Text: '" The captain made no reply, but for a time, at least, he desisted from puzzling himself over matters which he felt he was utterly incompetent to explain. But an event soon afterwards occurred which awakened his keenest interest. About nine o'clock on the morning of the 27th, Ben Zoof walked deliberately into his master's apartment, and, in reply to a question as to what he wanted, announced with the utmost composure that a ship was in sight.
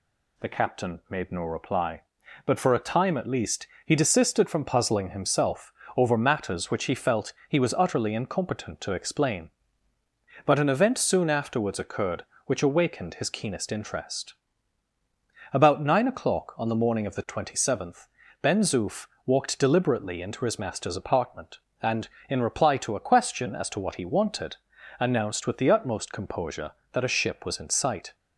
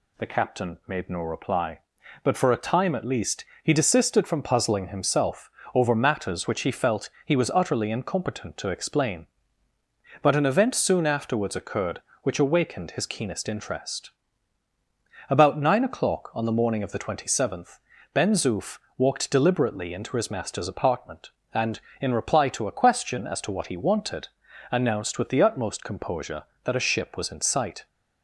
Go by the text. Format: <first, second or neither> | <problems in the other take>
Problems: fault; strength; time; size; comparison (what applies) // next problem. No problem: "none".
neither | pauses between "himself" and "over"; slight; the same in both // pauses between "felt" and "he"; slight; the same in both // pauses between "Zoof" and "walked"; slight; the same in both